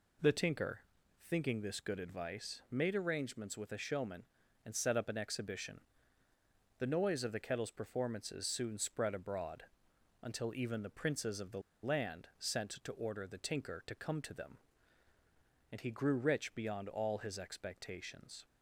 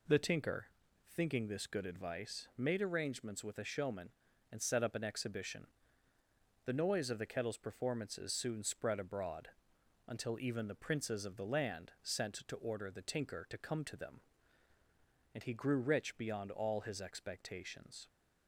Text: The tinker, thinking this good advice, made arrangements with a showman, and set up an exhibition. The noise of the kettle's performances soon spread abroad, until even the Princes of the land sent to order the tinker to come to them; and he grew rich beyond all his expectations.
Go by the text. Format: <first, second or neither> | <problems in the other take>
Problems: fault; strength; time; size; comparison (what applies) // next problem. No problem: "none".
second | pauses between "the" and "land"; slight; at 11.6 s; 0.22 s long